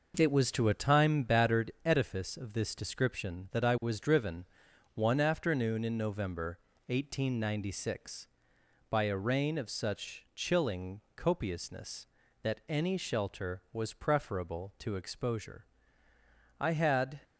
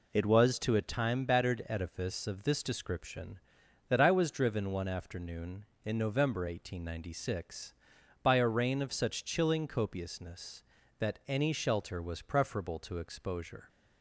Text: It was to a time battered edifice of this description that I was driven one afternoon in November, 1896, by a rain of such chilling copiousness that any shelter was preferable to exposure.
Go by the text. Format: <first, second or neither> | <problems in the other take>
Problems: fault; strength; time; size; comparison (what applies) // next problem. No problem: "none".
second | pauses between "driven" and "one"; noticeable; at 4.4 s; 0.48 s long // pauses between "chilling" and "copiousness"; slight; at 10.9 s; 0.16 s long // goes on to say "I had"; noticeable; from 16.5 s on; 0.62 s long